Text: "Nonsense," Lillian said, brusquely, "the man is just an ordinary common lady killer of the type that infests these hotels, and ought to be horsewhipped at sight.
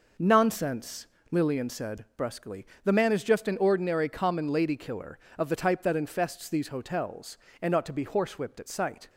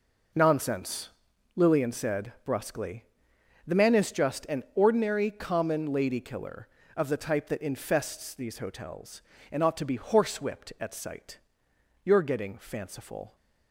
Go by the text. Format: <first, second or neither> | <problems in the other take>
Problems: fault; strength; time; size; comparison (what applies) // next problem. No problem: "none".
first | goes on to say "You're getting fanciful"; from 12.0 s on; 1.3 s long